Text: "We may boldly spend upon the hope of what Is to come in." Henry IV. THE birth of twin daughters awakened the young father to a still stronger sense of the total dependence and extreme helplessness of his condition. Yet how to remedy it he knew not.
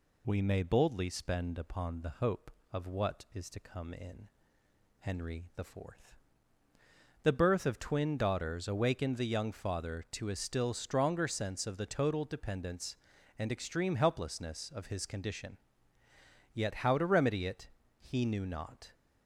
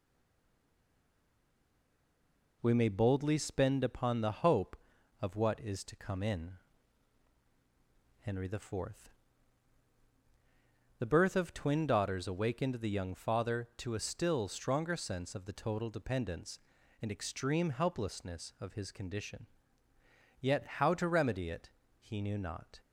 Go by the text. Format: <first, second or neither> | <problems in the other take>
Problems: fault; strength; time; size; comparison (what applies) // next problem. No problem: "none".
first | stays silent before the first word; strong; until 2.6 s; 2.6 s long // pauses between "it" and "he"; slight; at 21.7 s; 0.30 s long; slight in the first